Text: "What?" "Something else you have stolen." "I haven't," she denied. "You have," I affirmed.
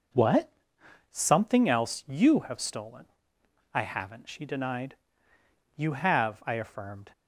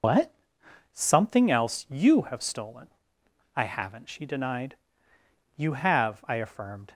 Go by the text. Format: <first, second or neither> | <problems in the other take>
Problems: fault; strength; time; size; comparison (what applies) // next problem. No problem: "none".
first | loses the start of "What"; at 0.0 s; 85 ms